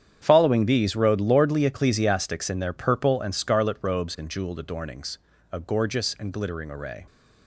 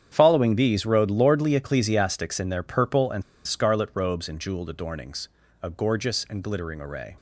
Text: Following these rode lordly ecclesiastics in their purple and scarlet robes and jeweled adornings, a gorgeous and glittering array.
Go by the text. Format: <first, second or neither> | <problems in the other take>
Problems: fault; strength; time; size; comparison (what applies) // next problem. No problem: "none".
first | starts louder than the rest; strong; until 1.1 s; 8.5 dB; strong in the first // pauses between "and" and "scarlet"; slight; at 3.2 s; 0.24 s long